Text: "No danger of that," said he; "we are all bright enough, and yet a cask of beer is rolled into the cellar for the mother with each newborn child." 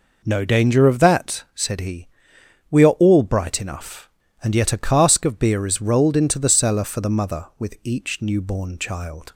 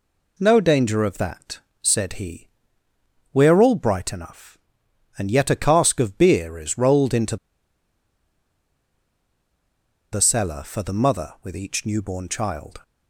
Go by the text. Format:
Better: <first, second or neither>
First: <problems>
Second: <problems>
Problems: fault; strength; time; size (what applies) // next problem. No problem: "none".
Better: first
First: none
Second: pauses between "into" and "the"; strong; at 7.3 s; 2.7 s long